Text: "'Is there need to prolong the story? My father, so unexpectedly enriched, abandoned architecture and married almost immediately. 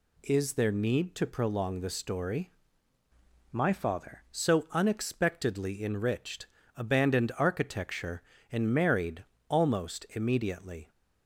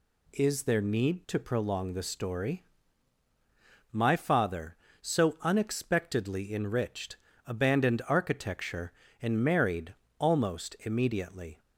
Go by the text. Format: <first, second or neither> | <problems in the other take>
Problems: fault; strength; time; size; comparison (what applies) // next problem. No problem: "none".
second | changes voice from "My" to "father"; from 3.5 to 4.2 s; 0.7 s long // pauses between "married" and "almost"; slight; at 9.2 s; 0.24 s long; slight in the second